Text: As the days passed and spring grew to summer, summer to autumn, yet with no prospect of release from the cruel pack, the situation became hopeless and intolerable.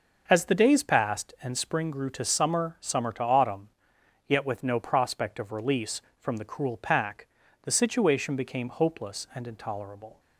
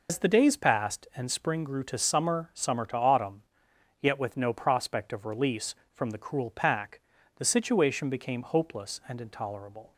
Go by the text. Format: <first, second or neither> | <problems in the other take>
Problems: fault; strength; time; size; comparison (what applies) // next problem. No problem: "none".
first | loses the start of "As"; at 0.0 s; 85 ms